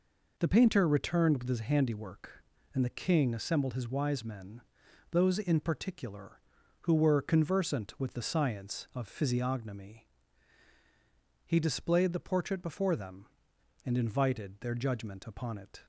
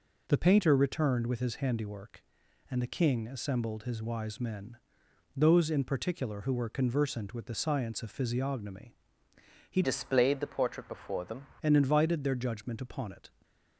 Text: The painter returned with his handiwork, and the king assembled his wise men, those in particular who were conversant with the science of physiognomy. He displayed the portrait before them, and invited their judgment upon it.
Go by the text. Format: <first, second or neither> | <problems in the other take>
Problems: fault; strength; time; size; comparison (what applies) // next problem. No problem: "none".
first | changes voice from "displayed" to "them"; from 9.8 to 11.4 s; 1.6 s long // stays silent after the last word; slight; from 13.2 s on; 0.5 s long